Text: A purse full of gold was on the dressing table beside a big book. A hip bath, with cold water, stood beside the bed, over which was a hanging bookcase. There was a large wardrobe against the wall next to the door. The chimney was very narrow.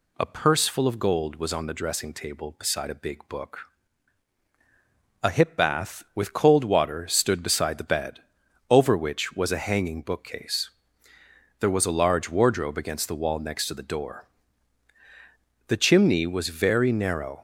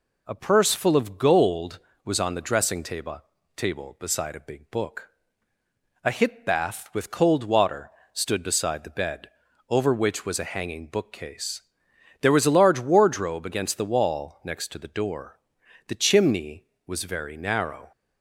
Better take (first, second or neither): first